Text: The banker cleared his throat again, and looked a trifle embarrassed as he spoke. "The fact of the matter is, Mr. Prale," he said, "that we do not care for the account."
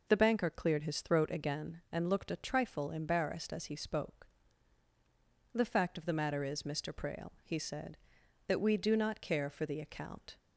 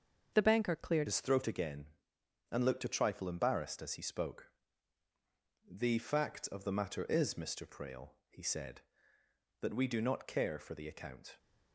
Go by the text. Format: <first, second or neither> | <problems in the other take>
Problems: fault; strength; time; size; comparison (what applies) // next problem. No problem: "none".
first | starts louder than the rest; until 1.3 s; 6.5 dB // changes voice at "his"; from 1.0 s on; 10.3 s long